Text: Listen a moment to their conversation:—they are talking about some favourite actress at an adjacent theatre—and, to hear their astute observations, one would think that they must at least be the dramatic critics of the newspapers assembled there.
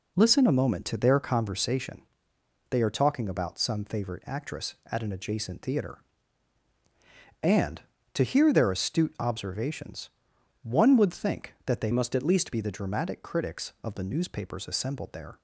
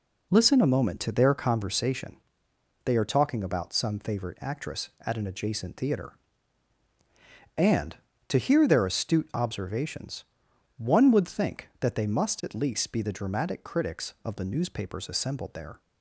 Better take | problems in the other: second | changes voice from "must" to "least"; from 11.9 to 12.5 s; 0.6 s long

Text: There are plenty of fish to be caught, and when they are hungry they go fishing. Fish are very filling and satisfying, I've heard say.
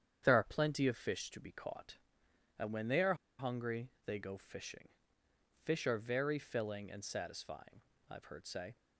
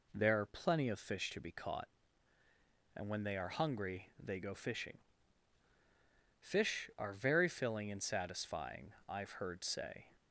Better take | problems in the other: second | starts louder than the rest; strong; until 1.2 s; 8.5 dB // pauses between "are" and "hungry"; slight; at 3.1 s; 0.24 s long // pauses between "hungry" and "they"; slight; at 3.8 s; 0.16 s long

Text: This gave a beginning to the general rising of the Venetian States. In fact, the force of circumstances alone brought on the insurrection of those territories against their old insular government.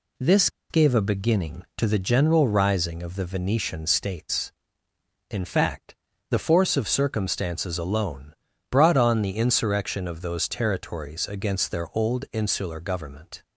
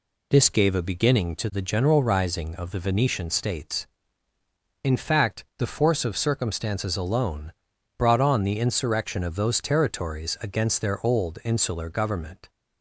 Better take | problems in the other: second | pauses between "This" and "gave"; slight; at 0.4 s; 0.22 s long // pauses between "alone" and "brought"; slight; at 8.3 s; 0.34 s long; also in the second

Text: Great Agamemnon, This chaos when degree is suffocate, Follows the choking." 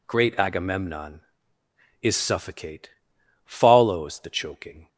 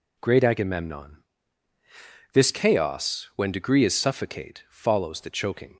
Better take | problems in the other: second | skips "This chaos when degree"; at 1.6 s

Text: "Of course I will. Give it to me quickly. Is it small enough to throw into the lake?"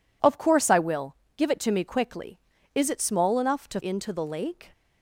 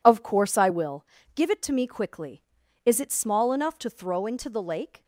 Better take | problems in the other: second | skips "throw"; at 3.7 s

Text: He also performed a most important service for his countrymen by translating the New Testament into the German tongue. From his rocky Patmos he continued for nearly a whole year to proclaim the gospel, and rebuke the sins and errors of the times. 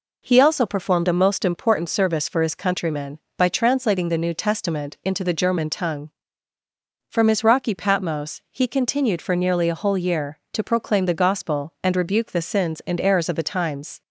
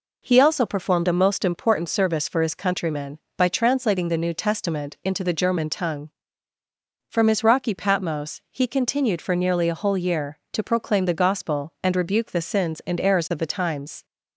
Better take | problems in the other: neither | none

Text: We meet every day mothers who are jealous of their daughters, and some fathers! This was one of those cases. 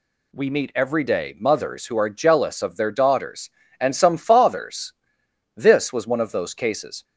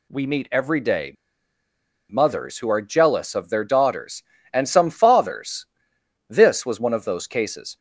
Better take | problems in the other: first | pauses between "day" and "mothers"; noticeable; at 1.1 s; 0.96 s long

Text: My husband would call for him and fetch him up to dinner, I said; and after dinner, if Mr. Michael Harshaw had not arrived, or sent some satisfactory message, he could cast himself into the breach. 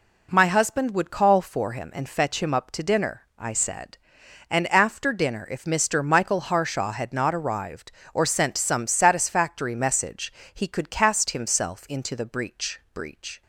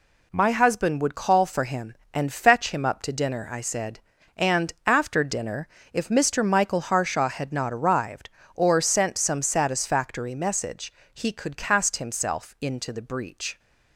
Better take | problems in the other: second | says "breach" twice; at 12.9 s

